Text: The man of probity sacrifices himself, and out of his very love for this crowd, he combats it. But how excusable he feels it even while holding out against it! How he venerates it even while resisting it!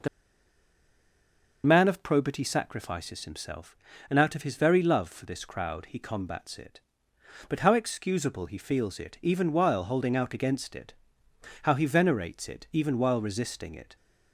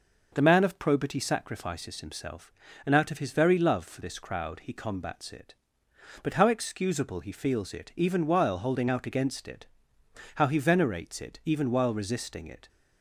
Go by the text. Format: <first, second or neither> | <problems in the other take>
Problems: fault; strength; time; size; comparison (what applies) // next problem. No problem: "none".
second | pauses between "The" and "man"; strong; at 0.0 s; 1.5 s long